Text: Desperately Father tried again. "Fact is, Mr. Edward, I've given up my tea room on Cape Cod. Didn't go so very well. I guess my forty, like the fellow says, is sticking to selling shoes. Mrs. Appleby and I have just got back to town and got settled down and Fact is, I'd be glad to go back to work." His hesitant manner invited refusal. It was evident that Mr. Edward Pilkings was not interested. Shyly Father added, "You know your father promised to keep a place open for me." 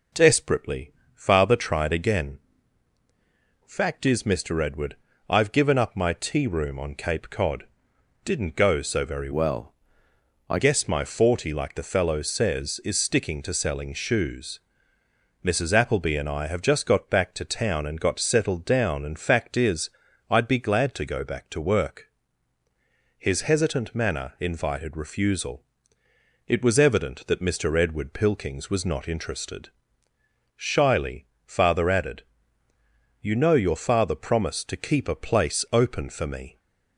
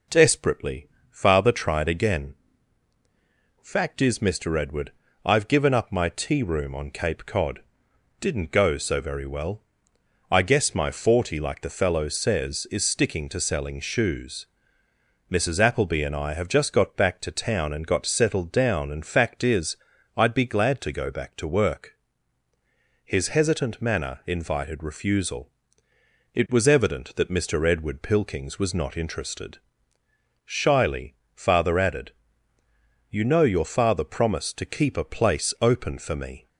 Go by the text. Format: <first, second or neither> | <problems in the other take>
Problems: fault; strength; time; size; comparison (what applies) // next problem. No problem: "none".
second | pauses between "Desperately" and "Father"; slight; at 0.9 s; 0.22 s long; slight in the second // changes voice from "well" to "I"; from 9.3 to 10.5 s; 1.2 s long // pauses between "Shyly" and "Father"; slight; at 31.2 s; 0.20 s long; slight in the second